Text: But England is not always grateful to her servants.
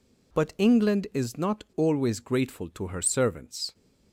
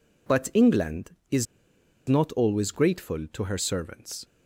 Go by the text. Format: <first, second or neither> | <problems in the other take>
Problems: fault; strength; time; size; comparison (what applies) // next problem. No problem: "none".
first | pauses between "is" and "not"; noticeable; at 1.4 s; 0.63 s long